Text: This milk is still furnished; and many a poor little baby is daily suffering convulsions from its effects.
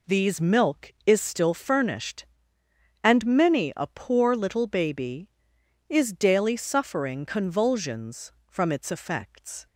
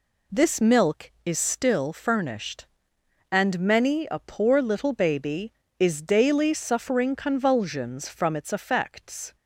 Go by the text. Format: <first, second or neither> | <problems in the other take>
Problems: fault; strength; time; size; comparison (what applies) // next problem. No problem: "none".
second | says "These" for "This"; at 0.0 s